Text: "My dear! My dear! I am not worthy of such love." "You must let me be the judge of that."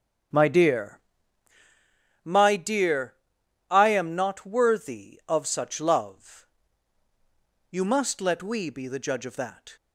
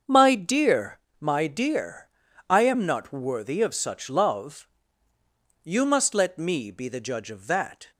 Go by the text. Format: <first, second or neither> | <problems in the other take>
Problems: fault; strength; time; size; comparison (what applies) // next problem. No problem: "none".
second | starts louder than the rest; strong; until 2.5 s; 7.5 dB; also in the second // says "we" for "me"; at 8.4 s